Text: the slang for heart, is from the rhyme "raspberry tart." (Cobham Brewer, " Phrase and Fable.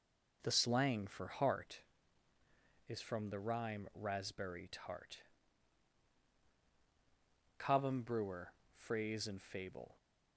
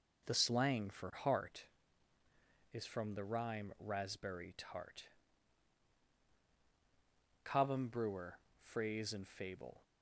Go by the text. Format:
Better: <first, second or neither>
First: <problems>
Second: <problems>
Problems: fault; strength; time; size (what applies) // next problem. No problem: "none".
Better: neither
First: none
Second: none